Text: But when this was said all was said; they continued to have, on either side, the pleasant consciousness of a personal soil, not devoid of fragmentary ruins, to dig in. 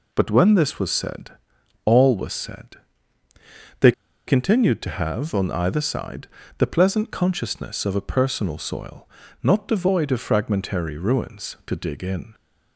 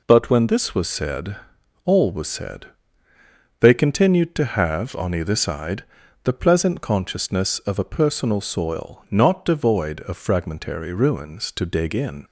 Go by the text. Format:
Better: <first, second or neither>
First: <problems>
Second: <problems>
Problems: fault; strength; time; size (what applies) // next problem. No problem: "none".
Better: second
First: pauses between "said" and "all"; noticeable; at 1.3 s; 0.54 s long // pauses between "they" and "continued"; at 3.8 s; 0.38 s long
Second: pauses between "said" and "all"; noticeable; at 1.3 s; 0.48 s long